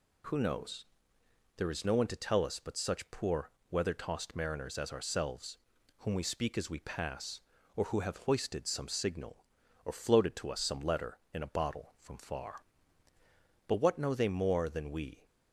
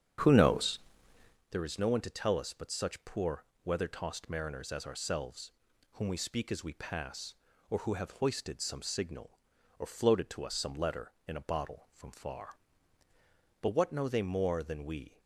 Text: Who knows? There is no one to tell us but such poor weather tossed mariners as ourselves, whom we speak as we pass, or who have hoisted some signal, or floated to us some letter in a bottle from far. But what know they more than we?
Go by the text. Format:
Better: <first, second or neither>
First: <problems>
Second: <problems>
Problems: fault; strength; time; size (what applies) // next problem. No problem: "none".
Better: first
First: pauses between "poor" and "weather"; slight; at 3.5 s; 0.18 s long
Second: starts louder than the rest; strong; until 1.4 s; 8.5 dB // pauses between "poor" and "weather"; slight; at 3.4 s; 0.18 s long